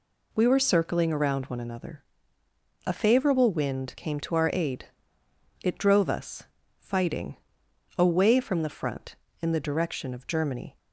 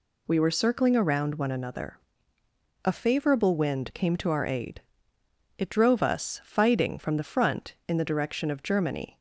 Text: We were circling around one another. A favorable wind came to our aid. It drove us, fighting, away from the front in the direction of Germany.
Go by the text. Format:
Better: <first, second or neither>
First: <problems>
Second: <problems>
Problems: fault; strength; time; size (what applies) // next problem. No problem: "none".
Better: first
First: none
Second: skips "away"; at 6.9 s